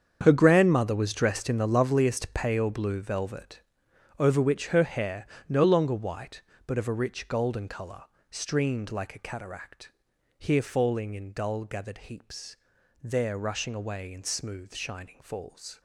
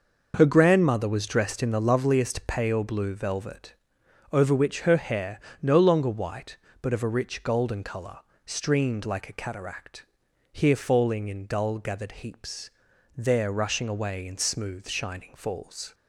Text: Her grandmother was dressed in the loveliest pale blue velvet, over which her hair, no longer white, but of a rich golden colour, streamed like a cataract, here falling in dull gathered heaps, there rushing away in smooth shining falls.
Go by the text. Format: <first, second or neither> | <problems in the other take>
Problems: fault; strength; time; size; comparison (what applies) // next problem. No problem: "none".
second | gets quieter; strong; throughout; 14 dB